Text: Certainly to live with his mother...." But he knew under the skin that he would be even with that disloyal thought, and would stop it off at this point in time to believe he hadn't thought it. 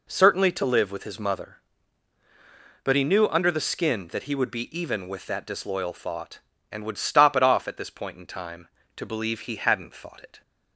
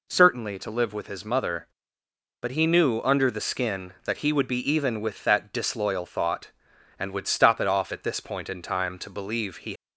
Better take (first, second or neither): first